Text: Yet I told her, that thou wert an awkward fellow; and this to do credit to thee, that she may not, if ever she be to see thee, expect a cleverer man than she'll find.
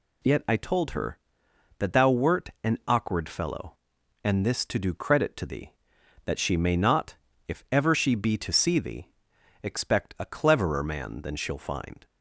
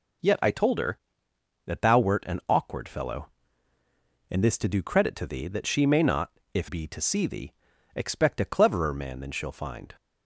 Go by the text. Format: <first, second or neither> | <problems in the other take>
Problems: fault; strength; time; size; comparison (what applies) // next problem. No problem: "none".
first | skips "ever she"; at 6.6 s